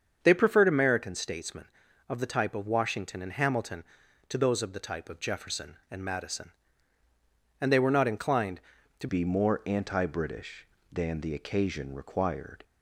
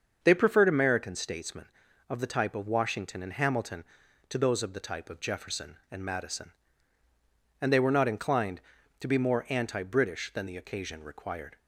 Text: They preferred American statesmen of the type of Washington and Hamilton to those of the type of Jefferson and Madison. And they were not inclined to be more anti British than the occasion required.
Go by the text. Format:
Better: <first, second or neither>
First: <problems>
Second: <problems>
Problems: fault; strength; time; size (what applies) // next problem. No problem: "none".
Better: second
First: starts louder than the rest; until 1.2 s; 7 dB // changes voice at "be"; from 9.0 s on; 3.6 s long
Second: starts louder than the rest; until 1.2 s; 6.5 dB